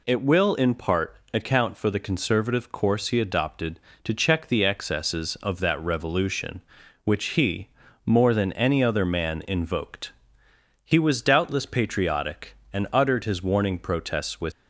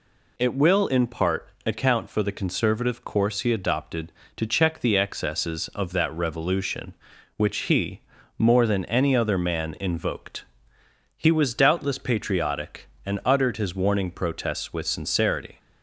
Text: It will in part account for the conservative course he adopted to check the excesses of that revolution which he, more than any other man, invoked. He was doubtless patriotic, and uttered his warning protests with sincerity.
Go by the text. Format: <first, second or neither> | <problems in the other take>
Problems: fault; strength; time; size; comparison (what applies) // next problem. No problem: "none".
second | pauses between "part" and "account"; slight; at 1.1 s; 0.16 s long; slight in the second // stops before "sincerity"; at 14.5 s